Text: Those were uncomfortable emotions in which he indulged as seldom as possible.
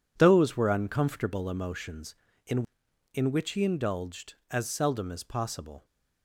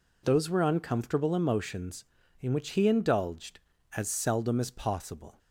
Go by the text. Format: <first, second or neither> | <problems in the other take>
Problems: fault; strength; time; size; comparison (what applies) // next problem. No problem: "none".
second | says "in" twice; at 3.1 s